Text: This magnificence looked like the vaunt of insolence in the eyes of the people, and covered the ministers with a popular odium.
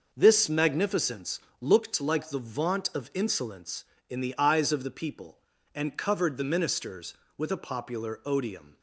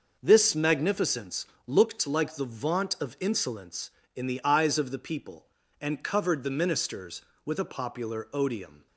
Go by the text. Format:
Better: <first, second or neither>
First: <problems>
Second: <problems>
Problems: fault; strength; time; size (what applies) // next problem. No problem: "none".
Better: neither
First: pauses between "magnificence" and "looked"; slight; at 1.3 s; 0.22 s long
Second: pauses between "magnificence" and "looked"; slight; at 1.4 s; 0.22 s long